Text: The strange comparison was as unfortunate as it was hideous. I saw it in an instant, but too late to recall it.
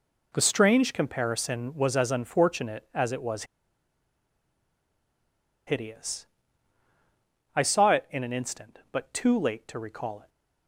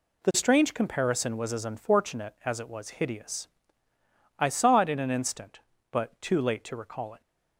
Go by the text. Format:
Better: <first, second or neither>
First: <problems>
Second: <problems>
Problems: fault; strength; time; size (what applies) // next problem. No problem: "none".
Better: second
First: pauses between "was" and "hideous"; strong; at 3.4 s; 2.2 s long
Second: none